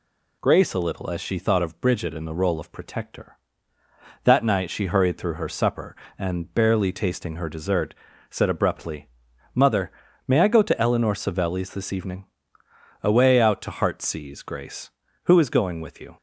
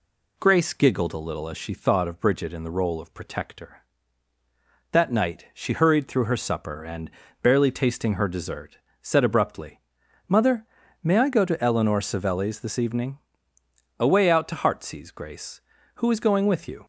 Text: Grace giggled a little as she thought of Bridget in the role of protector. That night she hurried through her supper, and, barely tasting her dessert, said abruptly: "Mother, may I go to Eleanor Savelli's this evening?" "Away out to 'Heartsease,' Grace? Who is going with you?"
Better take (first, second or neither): second